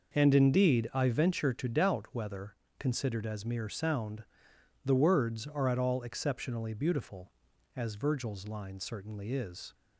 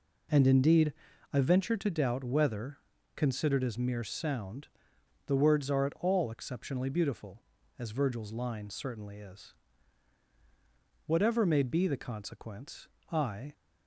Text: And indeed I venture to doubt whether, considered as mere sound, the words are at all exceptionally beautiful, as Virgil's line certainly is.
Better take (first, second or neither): first